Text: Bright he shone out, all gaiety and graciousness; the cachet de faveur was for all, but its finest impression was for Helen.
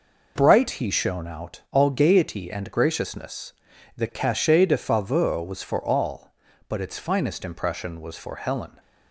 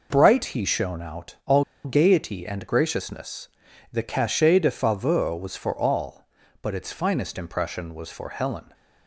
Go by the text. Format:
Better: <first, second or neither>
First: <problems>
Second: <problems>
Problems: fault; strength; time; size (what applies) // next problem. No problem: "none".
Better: first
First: none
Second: pauses between "all" and "gaiety"; slight; at 1.6 s; 0.21 s long